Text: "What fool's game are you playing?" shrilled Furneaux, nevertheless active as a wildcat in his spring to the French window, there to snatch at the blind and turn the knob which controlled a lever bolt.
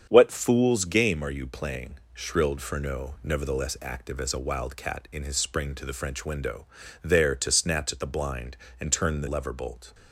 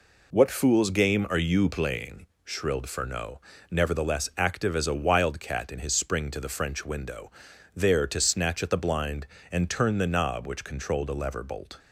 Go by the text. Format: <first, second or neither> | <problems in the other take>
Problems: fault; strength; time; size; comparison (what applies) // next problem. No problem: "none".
second | starts louder than the rest; strong; until 1.1 s; 7.5 dB // skips "knob which controlled a"; at 9.2 s